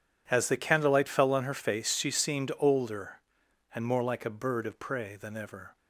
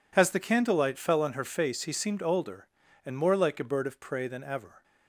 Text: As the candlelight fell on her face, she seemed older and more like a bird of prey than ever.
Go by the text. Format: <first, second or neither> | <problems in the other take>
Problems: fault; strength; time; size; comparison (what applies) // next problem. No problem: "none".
first | says "he" for "she"; at 1.8 s